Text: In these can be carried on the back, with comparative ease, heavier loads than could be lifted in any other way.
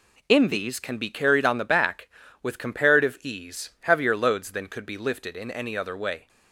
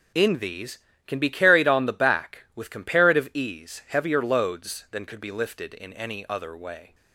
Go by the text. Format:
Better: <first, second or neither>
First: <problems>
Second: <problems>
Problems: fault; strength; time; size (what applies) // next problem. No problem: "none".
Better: neither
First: none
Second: none